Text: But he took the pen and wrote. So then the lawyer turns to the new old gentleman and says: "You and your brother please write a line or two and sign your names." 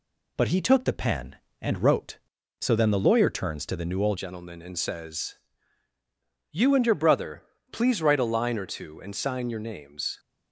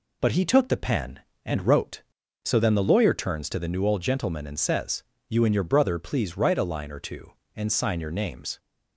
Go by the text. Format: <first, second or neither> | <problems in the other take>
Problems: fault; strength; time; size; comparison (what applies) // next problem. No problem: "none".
second | changes voice at "gentleman"; from 4.1 s on; 6.0 s long // pauses between "brother" and "please"; slight; at 7.4 s; 0.28 s long